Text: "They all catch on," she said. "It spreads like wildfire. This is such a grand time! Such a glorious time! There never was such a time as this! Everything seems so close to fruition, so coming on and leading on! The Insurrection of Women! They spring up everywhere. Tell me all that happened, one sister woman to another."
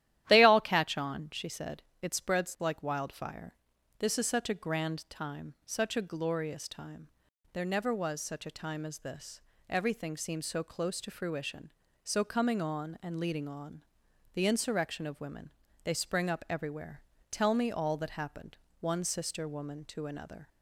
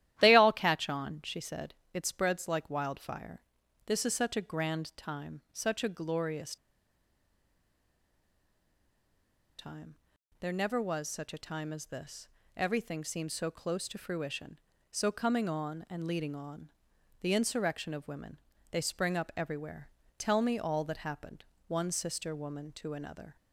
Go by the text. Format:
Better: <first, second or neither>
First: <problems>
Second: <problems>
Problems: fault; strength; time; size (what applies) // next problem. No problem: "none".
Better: first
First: starts louder than the rest; strong; until 1.2 s; 12.5 dB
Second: starts louder than the rest; strong; until 1.2 s; 12.5 dB // pauses between "glorious" and "time"; strong; at 6.5 s; 3.0 s long